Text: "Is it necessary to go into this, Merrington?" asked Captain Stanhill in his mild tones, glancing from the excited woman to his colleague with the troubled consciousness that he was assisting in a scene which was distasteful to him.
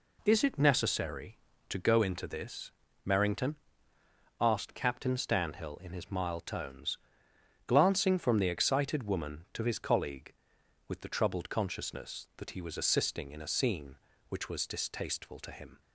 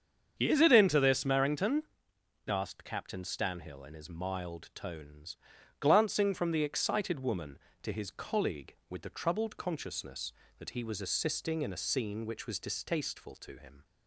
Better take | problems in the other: first | starts louder than the rest; strong; until 1.3 s; 7.5 dB // skips "necessary to go"; at 0.7 s

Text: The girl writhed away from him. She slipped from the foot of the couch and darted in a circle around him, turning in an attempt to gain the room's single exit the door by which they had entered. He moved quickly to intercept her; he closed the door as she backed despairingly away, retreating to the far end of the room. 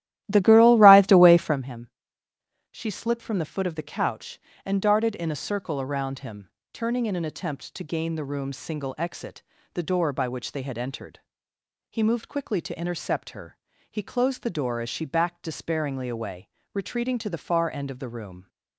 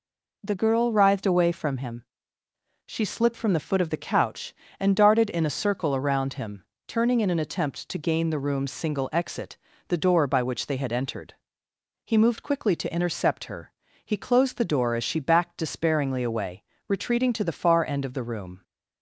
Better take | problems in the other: second | starts louder than the rest; strong; until 1.6 s; 14 dB // pauses between "exit" and "the"; slight; at 9.4 s; 0.32 s long; slight in the second

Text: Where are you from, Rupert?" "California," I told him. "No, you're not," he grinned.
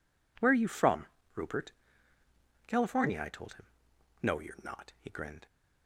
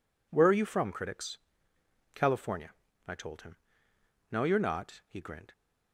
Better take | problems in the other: first | says "Critics" for "Rupert"; at 0.9 s

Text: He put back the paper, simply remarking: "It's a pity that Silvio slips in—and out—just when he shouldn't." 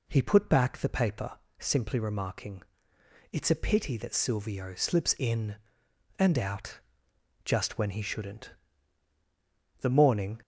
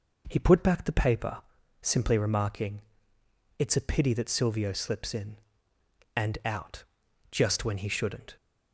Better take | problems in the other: second | goes on to say "The morning"; from 9.8 s on; 0.60 s long

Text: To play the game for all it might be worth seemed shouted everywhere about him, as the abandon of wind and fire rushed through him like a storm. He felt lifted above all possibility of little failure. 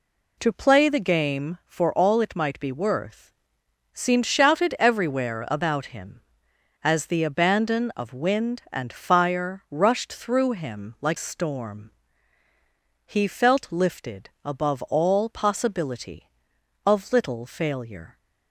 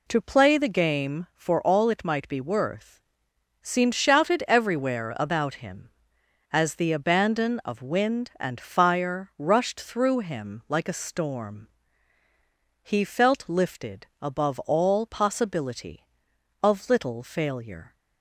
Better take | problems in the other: second | pauses between "worth" and "seemed"; noticeable; at 3.3 s; 0.60 s long; noticeable in the second // skips "a"; at 11.1 s // pauses between "lifted" and "above"; slight; at 14.2 s; 0.16 s long; slight in the second

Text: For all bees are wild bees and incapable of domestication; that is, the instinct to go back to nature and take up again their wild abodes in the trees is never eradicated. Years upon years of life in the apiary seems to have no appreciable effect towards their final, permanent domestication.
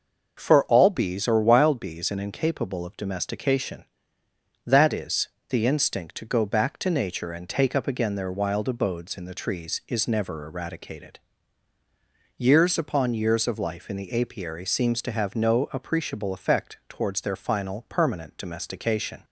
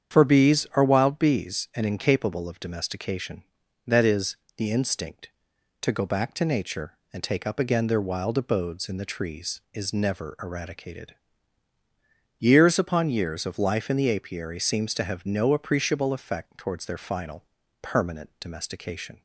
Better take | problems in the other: first | starts louder than the rest; strong; until 1.2 s; 8 dB; noticeable in the first // skips "all"; at 0.2 s

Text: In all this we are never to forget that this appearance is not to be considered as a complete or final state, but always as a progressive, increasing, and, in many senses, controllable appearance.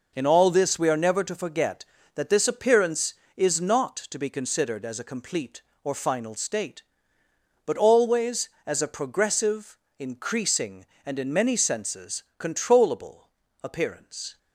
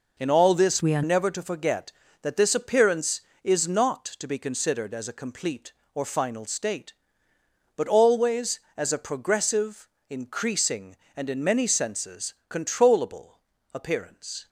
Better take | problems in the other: first | changes voice from "we" to "are"; from 0.8 to 1.0 s; 0.2 s long // pauses between "controllable" and "appearance"; slight; at 13.3 s; 0.34 s long; slight in the first

